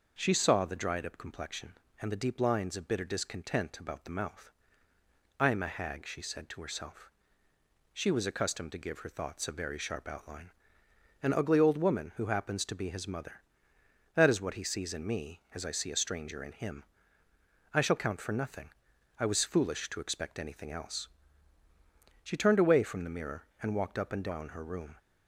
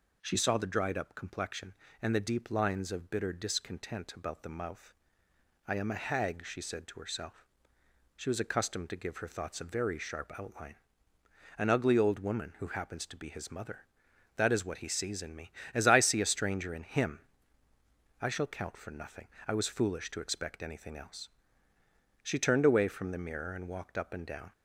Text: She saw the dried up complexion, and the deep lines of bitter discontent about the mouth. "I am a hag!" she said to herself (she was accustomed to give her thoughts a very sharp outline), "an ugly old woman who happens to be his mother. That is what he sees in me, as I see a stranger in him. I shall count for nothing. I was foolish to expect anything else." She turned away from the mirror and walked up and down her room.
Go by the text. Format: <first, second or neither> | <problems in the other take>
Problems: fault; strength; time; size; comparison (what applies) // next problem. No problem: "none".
first | stops before "her room"; at 24.5 s